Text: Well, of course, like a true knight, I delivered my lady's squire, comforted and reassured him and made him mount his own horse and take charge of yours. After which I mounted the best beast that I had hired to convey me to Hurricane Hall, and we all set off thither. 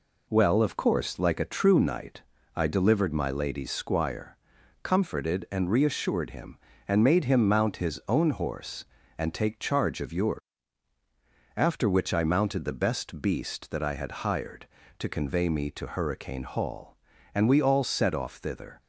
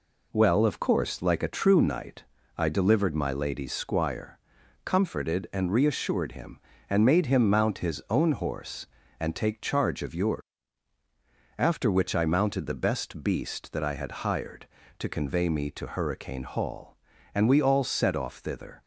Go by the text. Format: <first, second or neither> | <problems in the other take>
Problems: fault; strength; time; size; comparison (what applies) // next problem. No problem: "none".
neither | none